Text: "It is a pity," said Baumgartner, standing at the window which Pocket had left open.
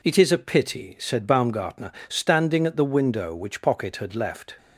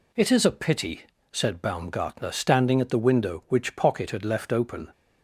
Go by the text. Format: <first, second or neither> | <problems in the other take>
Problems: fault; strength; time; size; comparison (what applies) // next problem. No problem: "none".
second | stops before "open"; at 4.5 s